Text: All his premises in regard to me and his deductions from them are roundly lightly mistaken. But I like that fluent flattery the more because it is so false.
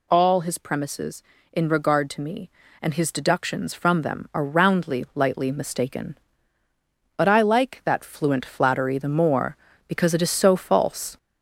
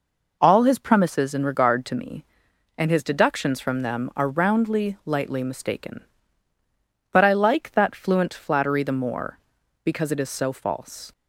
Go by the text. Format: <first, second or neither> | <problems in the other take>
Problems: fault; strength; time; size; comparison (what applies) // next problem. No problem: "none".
second | gets louder; slight; throughout; 3 dB